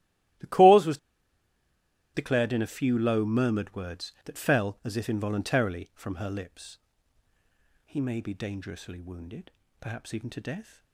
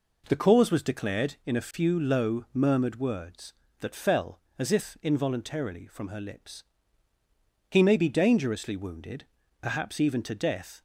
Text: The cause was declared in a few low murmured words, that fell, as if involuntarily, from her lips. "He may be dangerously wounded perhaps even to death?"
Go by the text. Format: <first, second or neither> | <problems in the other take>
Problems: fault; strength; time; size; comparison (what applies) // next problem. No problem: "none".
second | starts louder than the rest; strong; until 2.5 s; 15 dB // pauses between "was" and "declared"; at 0.9 s; 1.1 s long // pauses between "wounded" and "perhaps"; slight; at 9.4 s; 0.30 s long; slight in the second